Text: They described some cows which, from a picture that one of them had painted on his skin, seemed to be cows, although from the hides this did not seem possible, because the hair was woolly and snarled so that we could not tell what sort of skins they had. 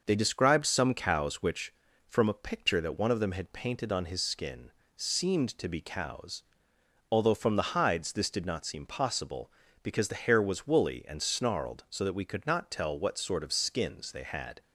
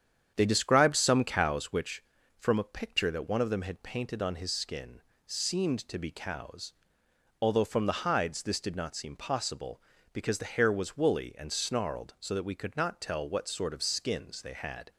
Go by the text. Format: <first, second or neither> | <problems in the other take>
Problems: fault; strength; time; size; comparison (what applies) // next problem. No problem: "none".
first | starts louder than the rest; strong; until 1.7 s; 8.5 dB